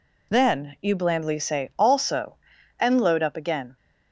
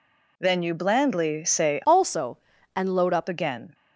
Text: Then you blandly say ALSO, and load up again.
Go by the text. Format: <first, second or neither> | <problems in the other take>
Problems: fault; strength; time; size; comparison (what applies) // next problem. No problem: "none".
first | changes voice from "ALSO" to "up"; from 1.8 to 3.2 s; 1.4 s long